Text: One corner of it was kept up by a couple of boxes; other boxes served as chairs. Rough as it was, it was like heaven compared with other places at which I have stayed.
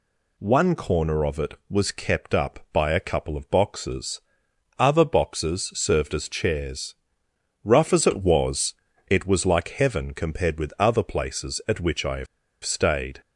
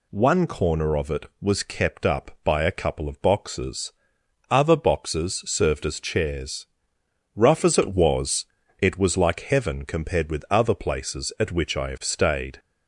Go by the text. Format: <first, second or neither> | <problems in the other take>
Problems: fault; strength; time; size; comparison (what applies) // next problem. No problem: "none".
second | pauses between "have" and "stayed"; at 12.2 s; 0.37 s long